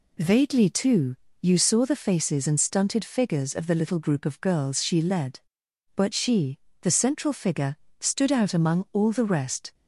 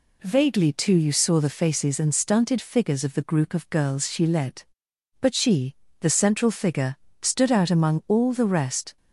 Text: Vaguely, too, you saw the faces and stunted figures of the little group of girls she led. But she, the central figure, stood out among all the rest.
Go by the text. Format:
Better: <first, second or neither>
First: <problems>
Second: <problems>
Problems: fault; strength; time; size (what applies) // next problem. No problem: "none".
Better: first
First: none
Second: skips "little"; at 3.2 s